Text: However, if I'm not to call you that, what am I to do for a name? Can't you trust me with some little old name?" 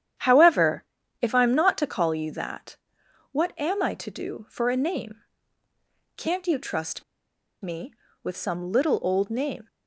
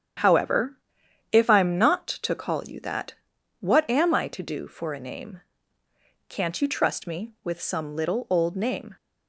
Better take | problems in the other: second | starts louder than the rest; strong; until 1.5 s; 9.5 dB; strong in the second // pauses between "trust" and "me"; noticeable; at 7.0 s; 0.59 s long

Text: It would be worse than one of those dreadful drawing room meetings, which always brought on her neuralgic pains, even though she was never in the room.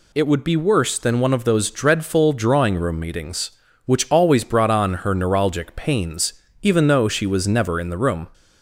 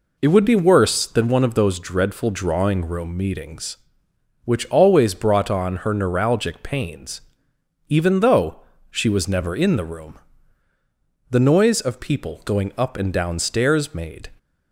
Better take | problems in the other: first | pauses between "though" and "she"; slight; at 8.5 s; 0.30 s long // goes on to say "The noise of people going up and down stairs made"; strong; from 11.2 s on; 3.0 s long

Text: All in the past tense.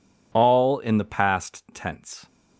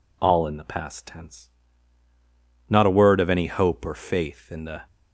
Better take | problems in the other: first | goes on to say "Not a word of any hope or faith in the"; strong; from 2.7 s on; 2.1 s long

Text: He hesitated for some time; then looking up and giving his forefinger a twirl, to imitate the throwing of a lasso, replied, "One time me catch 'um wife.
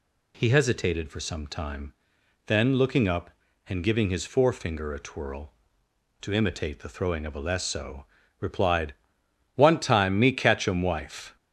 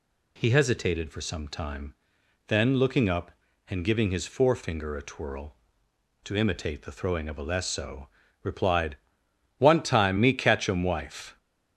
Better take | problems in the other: neither | none

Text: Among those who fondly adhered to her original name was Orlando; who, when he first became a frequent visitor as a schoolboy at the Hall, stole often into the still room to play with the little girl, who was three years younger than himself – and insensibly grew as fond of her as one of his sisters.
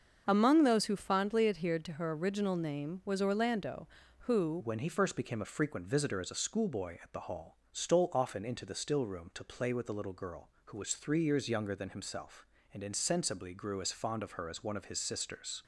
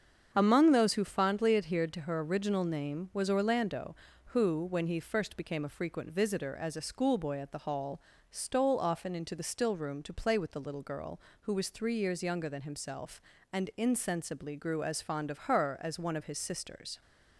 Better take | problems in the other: second | starts louder than the rest; until 1.2 s; 6.5 dB; strong in the second // changes voice at "when"; from 4.6 s on; 11.0 s long

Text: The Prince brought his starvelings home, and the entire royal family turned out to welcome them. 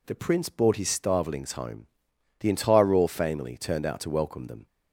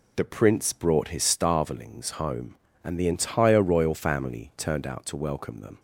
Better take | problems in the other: second | skips "and"; at 2.1 s

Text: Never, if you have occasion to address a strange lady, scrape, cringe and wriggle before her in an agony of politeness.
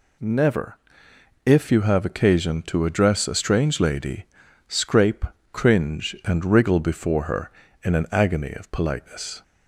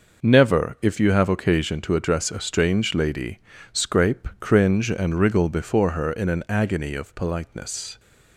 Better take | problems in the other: neither | none

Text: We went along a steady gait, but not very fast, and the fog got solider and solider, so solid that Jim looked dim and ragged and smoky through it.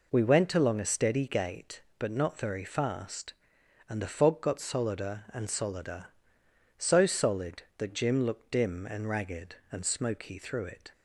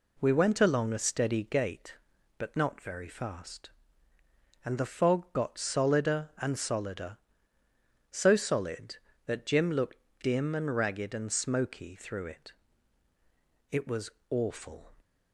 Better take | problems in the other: first | pauses between "looked" and "dim"; slight; at 9.9 s; 0.26 s long // goes on to say "It was awful"; noticeable; from 13.6 s on; 1.2 s long

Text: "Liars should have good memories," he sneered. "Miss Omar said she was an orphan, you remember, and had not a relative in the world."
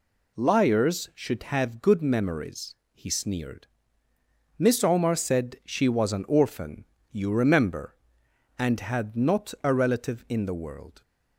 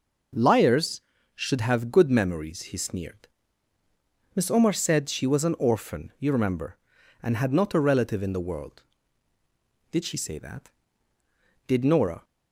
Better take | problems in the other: first | goes on to say "Did she say that Did Nora"; strong; from 9.9 s on; 2.3 s long

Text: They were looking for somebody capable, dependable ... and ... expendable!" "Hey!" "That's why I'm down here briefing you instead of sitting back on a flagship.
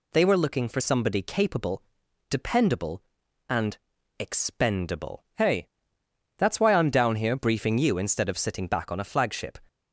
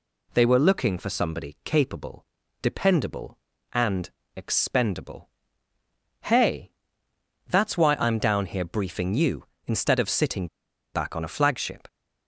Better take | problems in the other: first | pauses between "sitting" and "back"; noticeable; at 10.4 s; 0.48 s long

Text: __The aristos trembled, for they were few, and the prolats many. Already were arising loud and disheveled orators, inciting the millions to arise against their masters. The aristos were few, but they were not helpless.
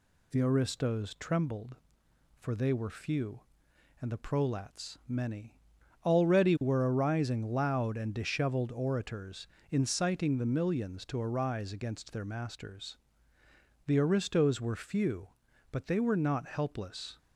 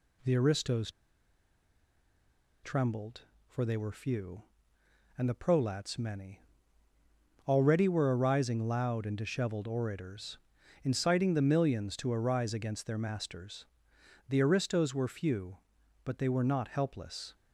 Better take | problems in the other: first | pauses between "aristos" and "trembled"; strong; at 0.9 s; 1.7 s long

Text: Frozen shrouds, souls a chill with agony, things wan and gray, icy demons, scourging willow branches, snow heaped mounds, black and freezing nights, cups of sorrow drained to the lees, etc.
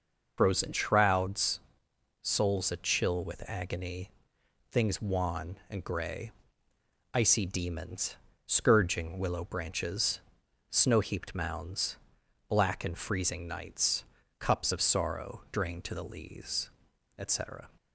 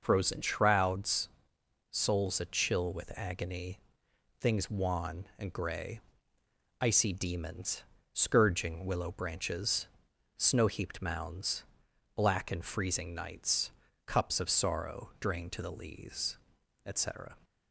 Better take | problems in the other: second | loses the start of "Frozen"; at 0.3 s; 45 ms

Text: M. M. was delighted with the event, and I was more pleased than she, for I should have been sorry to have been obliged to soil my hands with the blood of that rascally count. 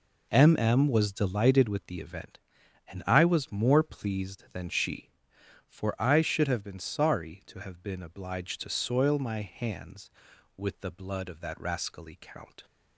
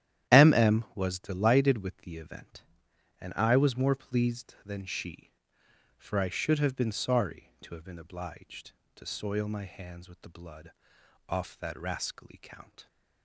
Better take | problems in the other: first | starts louder than the rest; strong; until 1.4 s; 11.5 dB // says "off" for "of"; at 11.2 s

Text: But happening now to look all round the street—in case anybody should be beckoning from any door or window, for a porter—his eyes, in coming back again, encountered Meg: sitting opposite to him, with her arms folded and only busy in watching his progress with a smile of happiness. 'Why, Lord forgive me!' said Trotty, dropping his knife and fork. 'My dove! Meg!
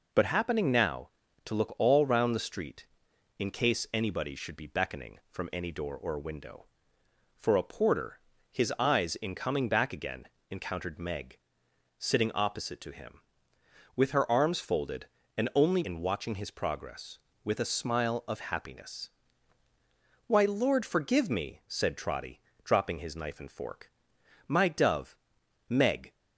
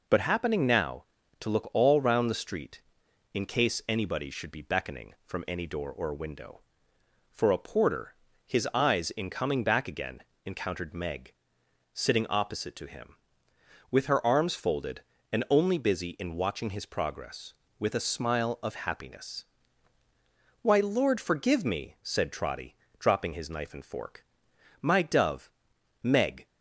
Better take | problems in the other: second | skips "busy"; at 15.8 s

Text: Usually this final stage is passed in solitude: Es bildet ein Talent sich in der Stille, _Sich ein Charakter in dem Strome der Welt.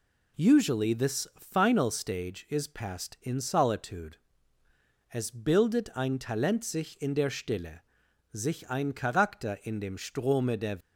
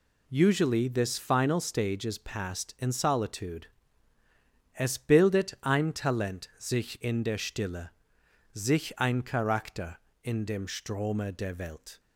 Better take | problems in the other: second | stops before "Welt"; at 10.8 s

